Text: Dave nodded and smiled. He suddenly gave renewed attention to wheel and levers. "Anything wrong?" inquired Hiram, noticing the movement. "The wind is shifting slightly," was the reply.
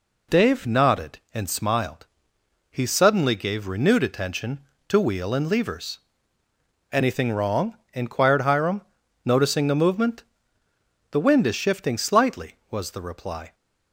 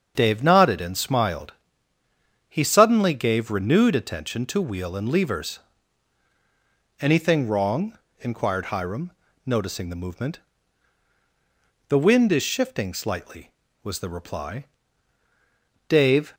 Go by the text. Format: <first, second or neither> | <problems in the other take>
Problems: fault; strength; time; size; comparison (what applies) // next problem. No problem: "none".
first | starts louder than the rest; until 1.1 s; 7 dB // goes on to say "Dave"; slight; from 15.8 s on; 0.46 s long